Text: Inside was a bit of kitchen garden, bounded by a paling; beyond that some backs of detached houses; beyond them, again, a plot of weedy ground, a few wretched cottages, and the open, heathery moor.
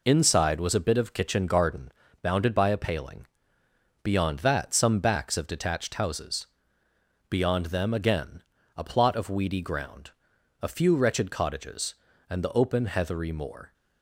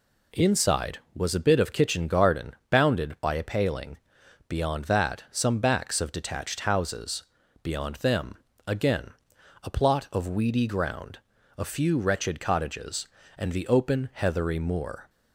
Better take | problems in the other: neither | none

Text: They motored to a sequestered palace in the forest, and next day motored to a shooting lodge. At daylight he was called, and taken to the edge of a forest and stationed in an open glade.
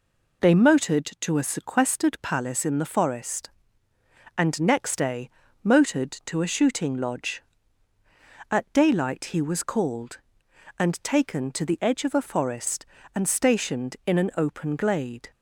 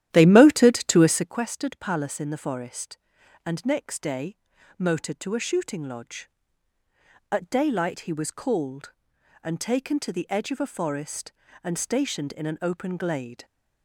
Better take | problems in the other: first | starts louder than the rest; strong; until 1.4 s; 12 dB // pauses between "day" and "motored"; at 4.3 s; 0.42 s long; slight in the first

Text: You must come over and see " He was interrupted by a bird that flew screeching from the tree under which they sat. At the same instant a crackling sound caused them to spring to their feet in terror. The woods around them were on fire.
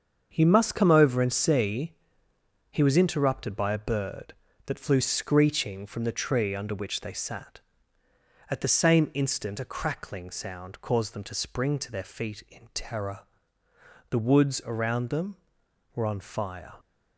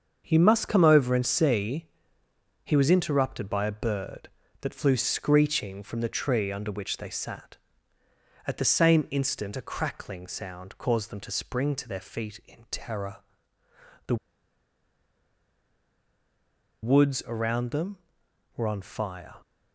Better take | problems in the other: first | starts louder than the rest; until 1.2 s; 6.5 dB; also in the first // pauses between "The" and "woods"; strong; at 14.1 s; 2.6 s long

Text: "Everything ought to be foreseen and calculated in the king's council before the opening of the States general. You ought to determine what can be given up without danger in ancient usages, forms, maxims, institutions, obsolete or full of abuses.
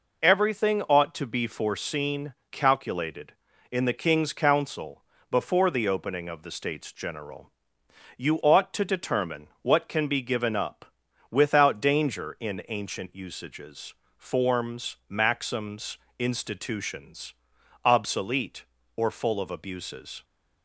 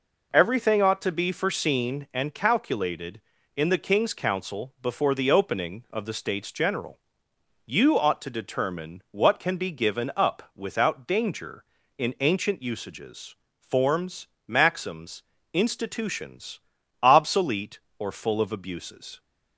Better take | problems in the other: second | skips "and"; at 2.4 s // pauses between "council" and "before"; slight; at 5.0 s; 0.28 s long // pauses between "up" and "without"; at 10.8 s; 0.44 s long

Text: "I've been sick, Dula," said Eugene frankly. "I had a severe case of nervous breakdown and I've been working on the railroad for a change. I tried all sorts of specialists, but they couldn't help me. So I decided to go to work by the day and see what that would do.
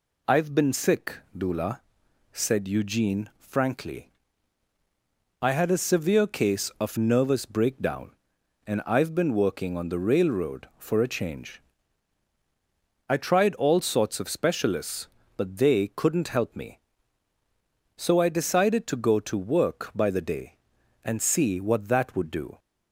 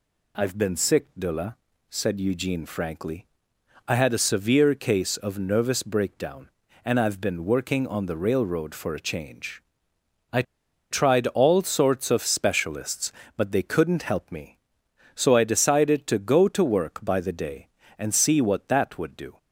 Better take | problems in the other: first | pauses between "I" and "tried"; noticeable; at 10.4 s; 0.48 s long

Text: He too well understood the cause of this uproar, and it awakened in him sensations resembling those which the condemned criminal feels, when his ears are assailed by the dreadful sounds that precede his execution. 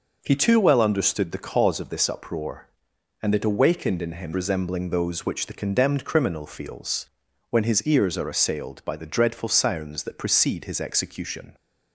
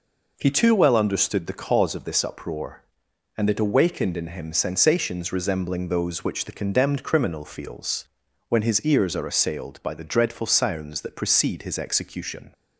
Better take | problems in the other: second | skips "sensations"; at 4.3 s

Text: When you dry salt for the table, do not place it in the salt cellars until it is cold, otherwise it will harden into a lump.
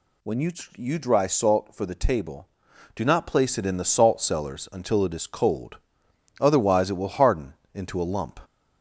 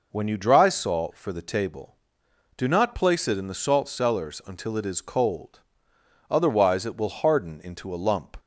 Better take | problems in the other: second | says "you" twice; at 0.7 s // pauses between "harden" and "into"; slight; at 7.5 s; 0.18 s long

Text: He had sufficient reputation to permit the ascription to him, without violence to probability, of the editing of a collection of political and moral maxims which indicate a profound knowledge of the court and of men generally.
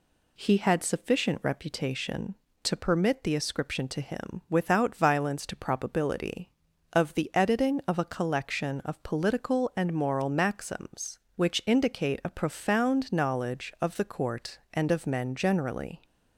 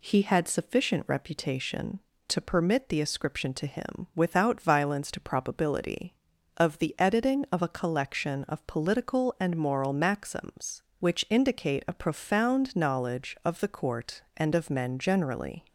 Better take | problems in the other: neither | none

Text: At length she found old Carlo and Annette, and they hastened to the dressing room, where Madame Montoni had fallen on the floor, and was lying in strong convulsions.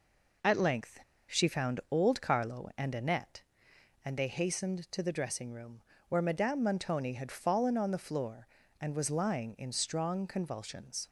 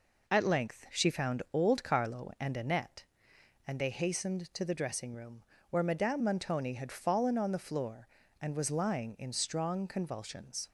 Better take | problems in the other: second | pauses between "length" and "she"; slight; at 0.9 s; 0.28 s long

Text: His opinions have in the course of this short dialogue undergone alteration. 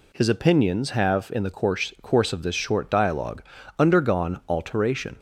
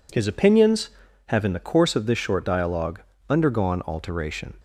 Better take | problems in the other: second | says "course" twice; at 2.0 s // pauses between "dialogue" and "undergone"; slight; at 3.4 s; 0.34 s long; slight in the second

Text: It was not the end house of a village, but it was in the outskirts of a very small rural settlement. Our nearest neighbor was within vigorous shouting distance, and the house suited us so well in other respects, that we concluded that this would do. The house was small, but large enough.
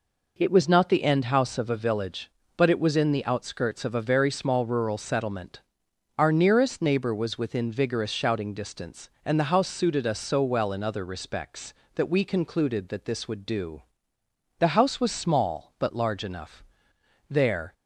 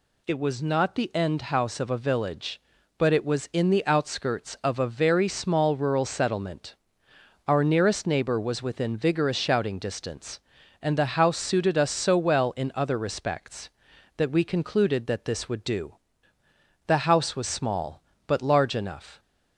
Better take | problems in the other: second | goes on to say "There"; slight; from 17.2 s on; 0.44 s long

